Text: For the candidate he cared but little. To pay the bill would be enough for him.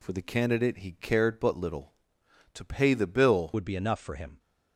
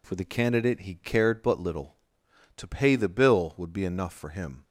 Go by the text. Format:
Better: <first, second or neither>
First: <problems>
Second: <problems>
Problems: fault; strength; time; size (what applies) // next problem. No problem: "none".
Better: second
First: changes voice at "would"; from 3.5 s on; 0.8 s long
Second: none